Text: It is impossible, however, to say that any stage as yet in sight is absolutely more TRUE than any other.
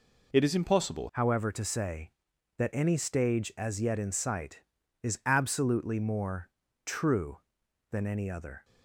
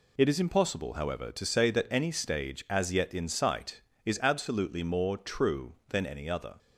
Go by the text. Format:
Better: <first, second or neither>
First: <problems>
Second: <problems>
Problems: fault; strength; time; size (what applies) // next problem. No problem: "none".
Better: second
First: changes voice at "however"; from 1.1 s on; 7.5 s long // pauses between "more" and "TRUE"; at 6.4 s; 0.38 s long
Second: none